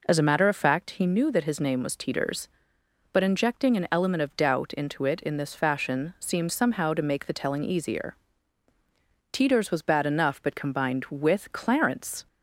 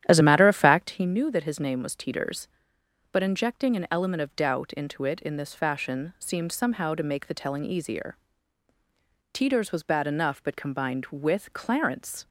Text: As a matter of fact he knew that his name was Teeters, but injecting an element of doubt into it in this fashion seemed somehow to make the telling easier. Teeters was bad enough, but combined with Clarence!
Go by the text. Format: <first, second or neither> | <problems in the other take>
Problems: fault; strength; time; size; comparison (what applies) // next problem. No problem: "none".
first | starts louder than the rest; strong; until 1.0 s; 11 dB